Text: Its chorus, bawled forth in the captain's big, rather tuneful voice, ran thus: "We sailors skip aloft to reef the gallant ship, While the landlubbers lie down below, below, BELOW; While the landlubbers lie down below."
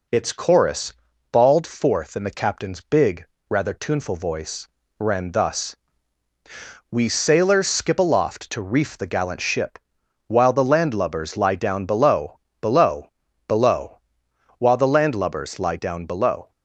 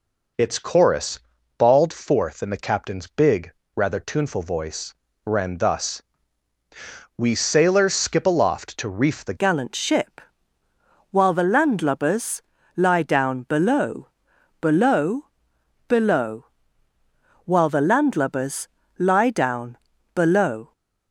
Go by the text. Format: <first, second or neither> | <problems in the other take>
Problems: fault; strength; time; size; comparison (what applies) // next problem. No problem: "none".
first | changes voice at "gallant"; from 9.3 s on; 11.4 s long // pauses between "landlubbers" and "lie"; at 12.3 s; 0.38 s long // pauses between "landlubbers" and "lie"; slight; at 18.6 s; 0.28 s long // pauses between "down" and "below"; at 19.7 s; 0.38 s long